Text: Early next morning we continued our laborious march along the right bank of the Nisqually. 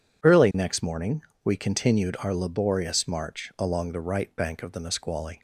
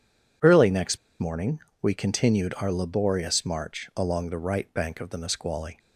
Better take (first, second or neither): first